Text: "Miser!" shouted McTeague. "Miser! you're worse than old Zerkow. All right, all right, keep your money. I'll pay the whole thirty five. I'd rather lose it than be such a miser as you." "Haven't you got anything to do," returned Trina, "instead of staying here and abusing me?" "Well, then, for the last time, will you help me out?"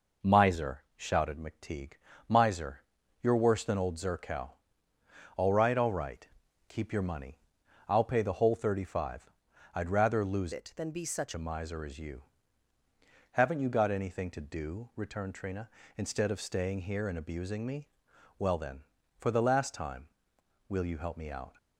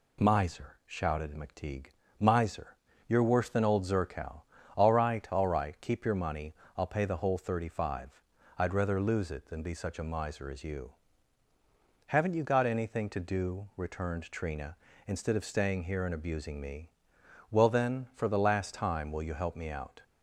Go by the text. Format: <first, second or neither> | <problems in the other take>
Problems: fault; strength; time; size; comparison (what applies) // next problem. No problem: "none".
second | changes voice from "it" to "such"; from 10.5 to 11.3 s; 0.8 s long